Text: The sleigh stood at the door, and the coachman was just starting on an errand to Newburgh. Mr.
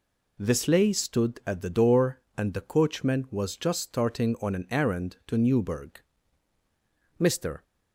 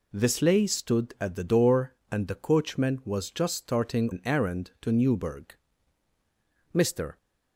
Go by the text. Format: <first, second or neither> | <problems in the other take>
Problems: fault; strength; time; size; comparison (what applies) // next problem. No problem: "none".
first | skips "on"; at 4.1 s